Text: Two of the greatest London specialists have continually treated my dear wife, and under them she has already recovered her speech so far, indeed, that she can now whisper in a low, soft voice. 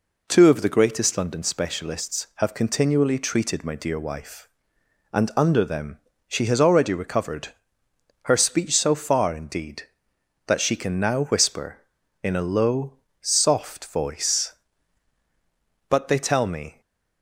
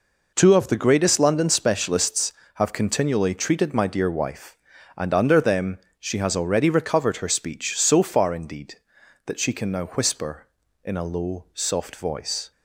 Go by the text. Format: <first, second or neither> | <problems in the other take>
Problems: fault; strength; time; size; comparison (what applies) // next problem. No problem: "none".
second | pauses between "them" and "she"; slight; at 5.9 s; 0.28 s long; slight in the second // pauses between "recovered" and "her"; noticeable; at 7.4 s; 0.74 s long // goes on to say "But they tell me"; noticeable; from 15.8 s on; 0.92 s long // stays silent after the last word; slight; from 16.7 s on; 0.5 s long